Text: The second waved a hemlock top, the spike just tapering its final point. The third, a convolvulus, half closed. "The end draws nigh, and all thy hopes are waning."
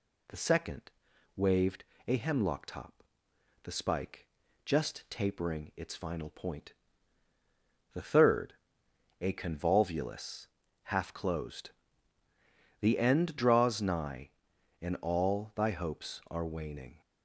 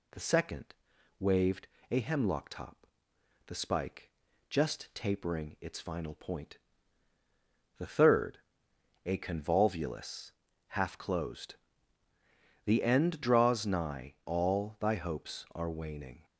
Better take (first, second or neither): first